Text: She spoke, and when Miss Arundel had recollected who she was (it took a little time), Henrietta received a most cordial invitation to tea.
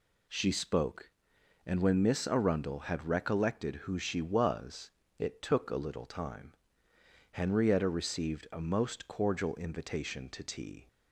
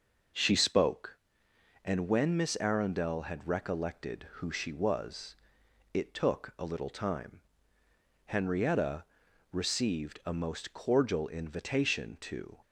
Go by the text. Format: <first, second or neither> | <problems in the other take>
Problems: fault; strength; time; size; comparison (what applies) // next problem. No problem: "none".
first | pauses between "Henrietta" and "received"; noticeable; at 9.0 s; 0.48 s long // stops before "tea"; at 12.6 s